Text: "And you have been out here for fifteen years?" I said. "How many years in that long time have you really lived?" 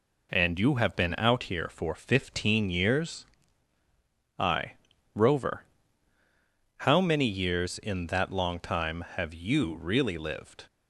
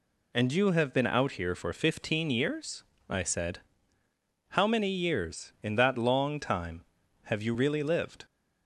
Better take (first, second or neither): second